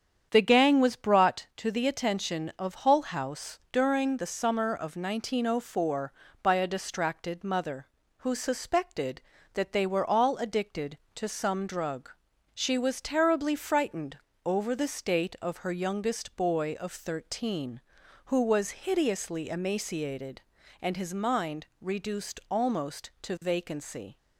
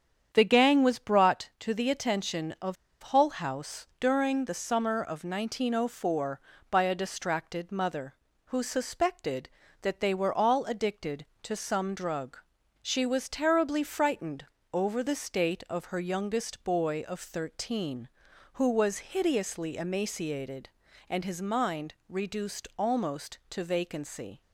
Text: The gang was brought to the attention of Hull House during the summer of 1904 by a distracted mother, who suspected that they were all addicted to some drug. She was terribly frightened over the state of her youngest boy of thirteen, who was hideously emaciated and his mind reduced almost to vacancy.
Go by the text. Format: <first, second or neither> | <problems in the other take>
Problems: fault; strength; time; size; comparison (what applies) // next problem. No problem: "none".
first | starts louder than the rest; strong; until 1.3 s; 8 dB; strong in the first // pauses between "of" and "Hull"; slight; at 2.7 s; 0.27 s long // pauses between "frightened" and "over"; slight; at 14.4 s; 0.26 s long; slight in the first // pauses between "mind" and "reduced"; slight; at 21.9 s; 0.16 s long; slight in the first